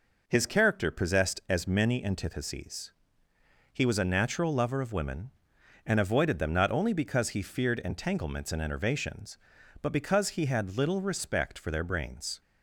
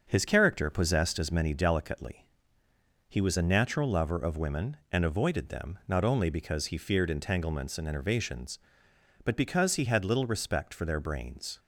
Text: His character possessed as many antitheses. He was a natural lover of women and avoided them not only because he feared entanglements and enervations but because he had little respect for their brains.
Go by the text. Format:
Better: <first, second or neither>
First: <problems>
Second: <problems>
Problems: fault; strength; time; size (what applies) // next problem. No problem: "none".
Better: first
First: none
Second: starts louder than the rest; until 1.0 s; 6.5 dB // says "delicately" for "antitheses"; at 1.5 s